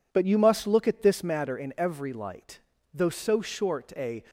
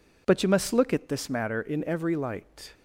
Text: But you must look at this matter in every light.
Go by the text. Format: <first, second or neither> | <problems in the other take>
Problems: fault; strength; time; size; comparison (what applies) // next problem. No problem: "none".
second | goes on to say "Though so short a"; noticeable; from 2.9 s on; 1.3 s long